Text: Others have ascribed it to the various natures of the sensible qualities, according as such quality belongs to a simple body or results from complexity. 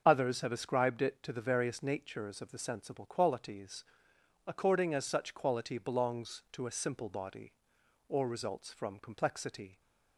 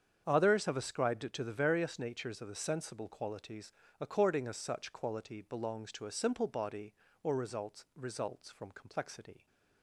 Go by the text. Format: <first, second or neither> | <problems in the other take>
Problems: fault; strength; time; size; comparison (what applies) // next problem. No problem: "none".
first | starts louder than the rest; strong; until 1.2 s; 7.5 dB; also in the first // says "results" twice; at 7.9 s